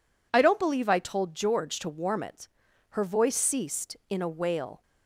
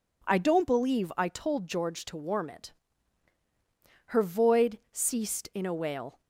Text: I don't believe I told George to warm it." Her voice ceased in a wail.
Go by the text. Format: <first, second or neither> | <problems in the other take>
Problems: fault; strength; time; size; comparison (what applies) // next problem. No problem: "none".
first | says "void" for "voice"; at 4.2 s